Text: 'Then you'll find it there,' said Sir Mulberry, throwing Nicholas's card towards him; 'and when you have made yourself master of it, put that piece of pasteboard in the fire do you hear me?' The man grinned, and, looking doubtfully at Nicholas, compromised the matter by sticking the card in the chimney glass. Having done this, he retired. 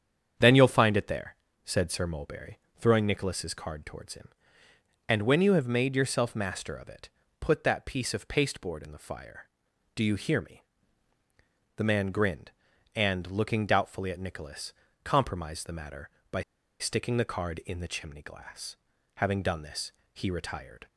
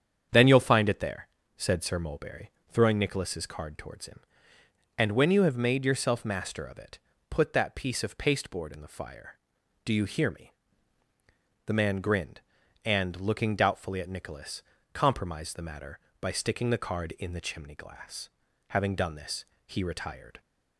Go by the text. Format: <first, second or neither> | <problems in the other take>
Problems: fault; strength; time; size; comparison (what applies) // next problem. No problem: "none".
second | starts louder than the rest; strong; until 1.6 s; 8 dB; strong in the second // pauses between "by" and "sticking"; at 16.4 s; 0.37 s long